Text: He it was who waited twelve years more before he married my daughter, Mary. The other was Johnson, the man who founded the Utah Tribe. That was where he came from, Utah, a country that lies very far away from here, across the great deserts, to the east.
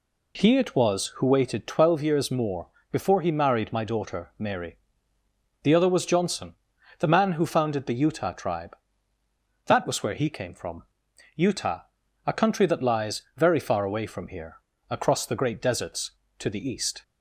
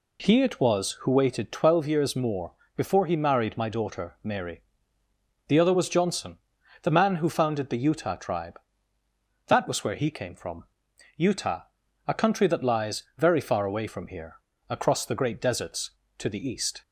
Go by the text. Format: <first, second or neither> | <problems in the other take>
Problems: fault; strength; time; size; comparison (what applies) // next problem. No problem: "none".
neither | pauses between "more" and "before"; slight; the same in both